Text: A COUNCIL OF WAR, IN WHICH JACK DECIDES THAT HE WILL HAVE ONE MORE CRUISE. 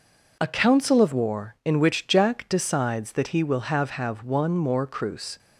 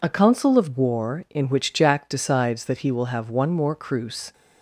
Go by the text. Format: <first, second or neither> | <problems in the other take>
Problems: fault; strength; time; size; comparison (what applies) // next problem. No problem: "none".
second | says "HAVE" twice; at 3.8 s